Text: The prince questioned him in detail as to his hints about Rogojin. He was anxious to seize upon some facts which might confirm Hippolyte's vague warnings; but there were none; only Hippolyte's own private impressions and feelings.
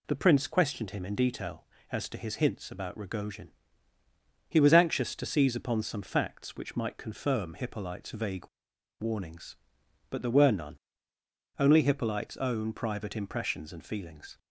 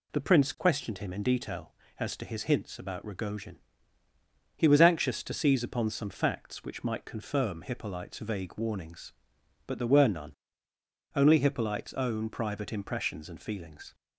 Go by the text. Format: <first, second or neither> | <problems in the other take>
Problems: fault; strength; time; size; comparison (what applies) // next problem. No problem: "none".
second | pauses between "vague" and "warnings"; noticeable; at 8.4 s; 0.51 s long